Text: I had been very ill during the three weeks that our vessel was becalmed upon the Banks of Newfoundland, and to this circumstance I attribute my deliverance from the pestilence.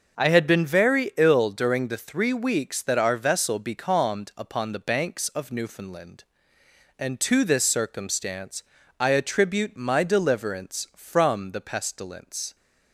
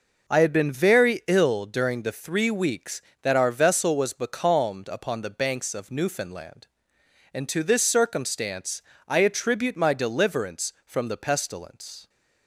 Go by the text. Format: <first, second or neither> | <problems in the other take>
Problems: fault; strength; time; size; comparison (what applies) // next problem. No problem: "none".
second | starts louder than the rest; noticeable; until 1.2 s; 6 dB // skips "was"; at 3.5 s // pauses between "circumstance" and "I"; slight; at 8.6 s; 0.34 s long; slight in the second